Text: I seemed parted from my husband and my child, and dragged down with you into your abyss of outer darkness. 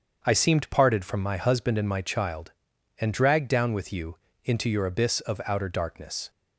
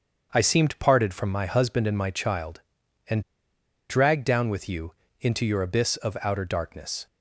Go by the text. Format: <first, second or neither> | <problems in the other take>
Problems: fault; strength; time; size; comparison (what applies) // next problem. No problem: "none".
first | starts louder than the rest; until 1.3 s; 7 dB; also in the first // pauses between "and" and "dragged"; noticeable; at 3.1 s; 0.70 s long // pauses between "you" and "into"; slight; at 4.9 s; 0.28 s long; slight in the first